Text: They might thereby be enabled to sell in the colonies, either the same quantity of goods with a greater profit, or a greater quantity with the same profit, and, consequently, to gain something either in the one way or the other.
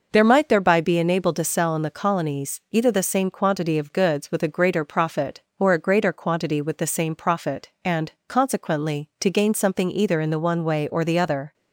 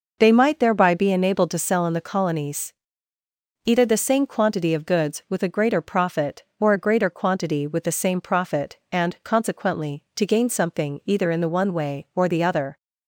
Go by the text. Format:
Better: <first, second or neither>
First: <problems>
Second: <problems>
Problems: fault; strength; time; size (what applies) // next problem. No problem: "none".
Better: second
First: says "There" for "They"; at 0.1 s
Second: none